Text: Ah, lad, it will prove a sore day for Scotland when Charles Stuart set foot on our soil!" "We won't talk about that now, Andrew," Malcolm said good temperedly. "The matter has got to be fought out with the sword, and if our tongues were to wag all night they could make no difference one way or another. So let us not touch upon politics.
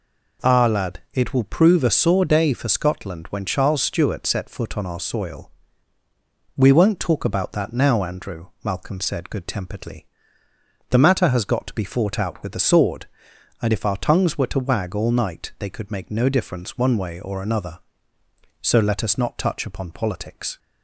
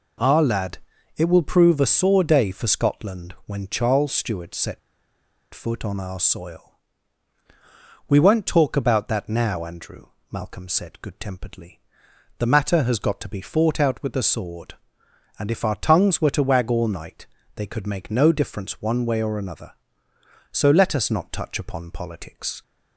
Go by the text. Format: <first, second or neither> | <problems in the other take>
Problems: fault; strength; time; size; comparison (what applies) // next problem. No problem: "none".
first | pauses between "set" and "foot"; noticeable; at 4.7 s; 0.74 s long // pauses between "night" and "they"; slight; at 17.2 s; 0.28 s long